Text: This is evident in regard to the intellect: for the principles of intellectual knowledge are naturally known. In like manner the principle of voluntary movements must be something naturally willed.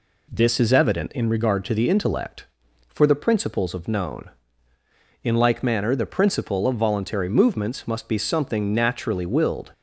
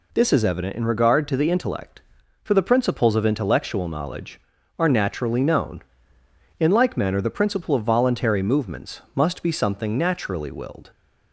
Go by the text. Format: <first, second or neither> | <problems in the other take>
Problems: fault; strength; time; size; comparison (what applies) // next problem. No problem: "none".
second | skips "intellectual knowledge are naturally"; at 3.8 s